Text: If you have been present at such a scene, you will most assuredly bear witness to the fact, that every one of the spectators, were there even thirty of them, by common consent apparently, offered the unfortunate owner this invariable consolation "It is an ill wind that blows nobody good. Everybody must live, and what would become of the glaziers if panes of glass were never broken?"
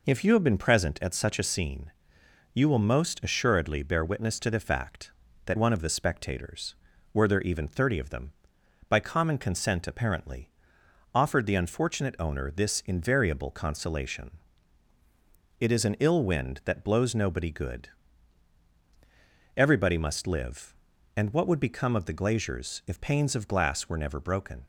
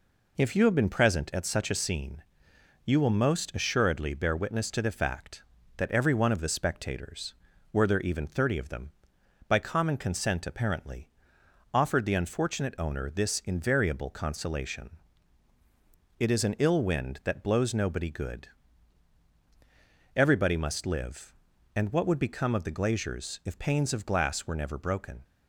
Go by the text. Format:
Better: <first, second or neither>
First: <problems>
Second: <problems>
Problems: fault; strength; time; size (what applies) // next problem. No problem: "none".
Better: second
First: skips "every"; at 5.5 s // pauses between "consolation" and "It"; strong; at 14.3 s; 1.3 s long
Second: pauses between "consolation" and "It"; strong; at 14.9 s; 1.3 s long